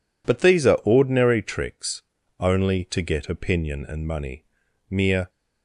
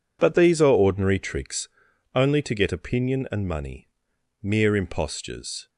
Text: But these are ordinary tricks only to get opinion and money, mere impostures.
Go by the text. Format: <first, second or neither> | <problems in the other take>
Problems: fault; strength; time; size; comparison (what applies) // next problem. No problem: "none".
second | pauses between "tricks" and "only"; at 2.0 s; 0.37 s long; also in the second // stops before "impostures"; at 5.2 s